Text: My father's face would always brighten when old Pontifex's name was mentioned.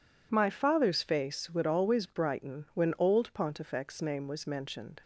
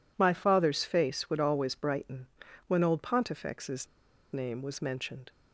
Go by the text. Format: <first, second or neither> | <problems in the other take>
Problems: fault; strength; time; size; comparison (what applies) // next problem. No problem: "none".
first | pauses between "brighten" and "when"; at 2.2 s; 0.40 s long // pauses between "Pontifex's" and "name"; noticeable; at 3.8 s; 0.47 s long